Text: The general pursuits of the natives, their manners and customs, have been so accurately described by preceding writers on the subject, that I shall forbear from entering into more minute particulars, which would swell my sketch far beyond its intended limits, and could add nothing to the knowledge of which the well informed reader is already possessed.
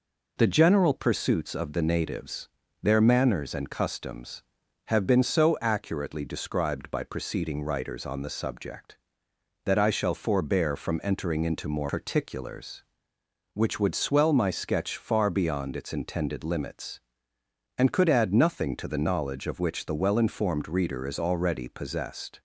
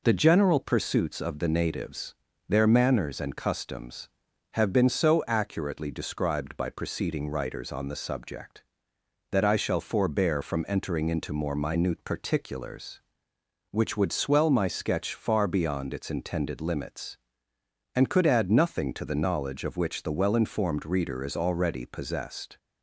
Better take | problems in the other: second | skips "minute"; at 11.8 s

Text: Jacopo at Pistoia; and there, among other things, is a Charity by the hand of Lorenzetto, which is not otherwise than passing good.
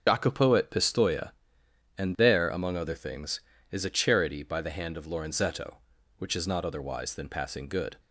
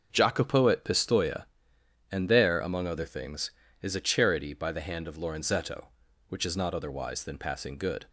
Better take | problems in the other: second | loses the start of "Jacopo"; at 0.0 s; 90 ms // starts louder than the rest; until 1.0 s; 6.5 dB; also in the second

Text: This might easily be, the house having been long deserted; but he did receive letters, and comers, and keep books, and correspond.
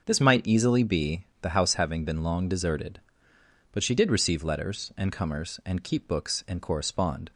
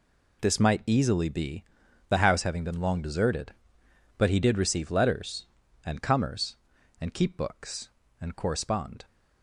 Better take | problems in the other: second | starts louder than the rest; noticeable; until 1.0 s; 6 dB // says "she" for "he"; at 3.8 s

